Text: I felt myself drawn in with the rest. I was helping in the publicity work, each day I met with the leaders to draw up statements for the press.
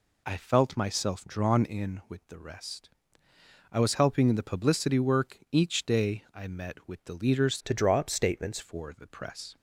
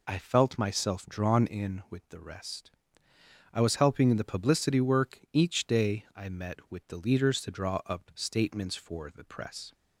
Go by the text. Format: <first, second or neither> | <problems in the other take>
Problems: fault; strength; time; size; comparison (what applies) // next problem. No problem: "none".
second | changes voice from "to" to "statements"; from 7.6 to 8.5 s; 0.9 s long